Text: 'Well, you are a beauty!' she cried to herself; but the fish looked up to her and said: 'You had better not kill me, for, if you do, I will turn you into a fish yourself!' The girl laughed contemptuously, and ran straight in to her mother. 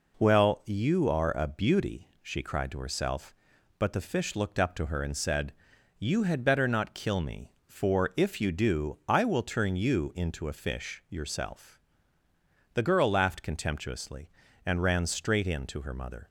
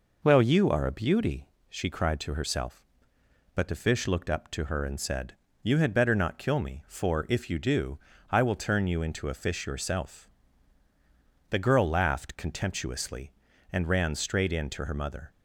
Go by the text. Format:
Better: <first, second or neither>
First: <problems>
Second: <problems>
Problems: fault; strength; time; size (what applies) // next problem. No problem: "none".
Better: neither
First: none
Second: none